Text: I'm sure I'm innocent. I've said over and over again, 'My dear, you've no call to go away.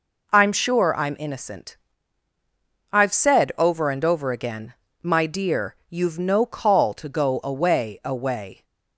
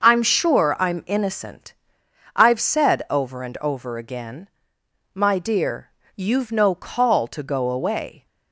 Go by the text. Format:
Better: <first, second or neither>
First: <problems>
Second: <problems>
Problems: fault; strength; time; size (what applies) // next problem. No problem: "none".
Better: second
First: says "away" twice; at 8.0 s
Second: none